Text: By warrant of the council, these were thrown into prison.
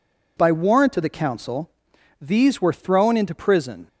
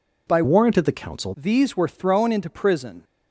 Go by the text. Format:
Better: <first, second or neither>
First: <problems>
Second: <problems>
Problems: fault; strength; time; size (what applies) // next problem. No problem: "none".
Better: first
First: none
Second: changes voice from "warrant" to "council"; from 0.4 to 1.3 s; 0.9 s long